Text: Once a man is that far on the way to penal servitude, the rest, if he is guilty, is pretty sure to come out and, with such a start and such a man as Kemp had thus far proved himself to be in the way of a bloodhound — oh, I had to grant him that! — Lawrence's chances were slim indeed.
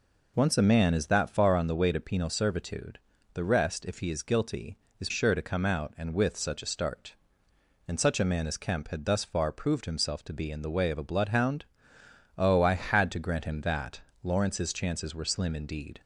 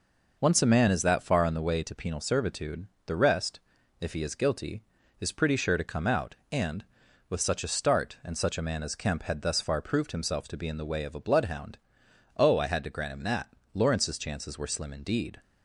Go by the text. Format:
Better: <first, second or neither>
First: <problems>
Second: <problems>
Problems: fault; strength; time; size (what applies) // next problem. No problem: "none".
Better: second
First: skips "pretty"; at 5.0 s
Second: none